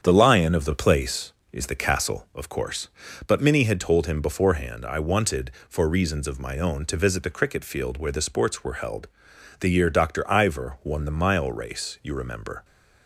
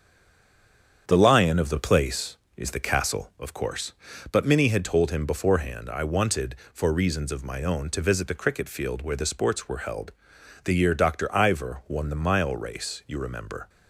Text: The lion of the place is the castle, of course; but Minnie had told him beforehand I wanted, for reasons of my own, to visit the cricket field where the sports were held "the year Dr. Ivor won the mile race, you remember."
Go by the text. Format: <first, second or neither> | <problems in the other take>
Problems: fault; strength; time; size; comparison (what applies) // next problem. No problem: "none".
first | stays silent before the first word; until 1.0 s; 1.0 s long // starts louder than the rest; strong; until 2.0 s; 8 dB; strong in the first // pauses between "held" and "the"; noticeable; at 10.1 s; 0.54 s long; noticeable in the first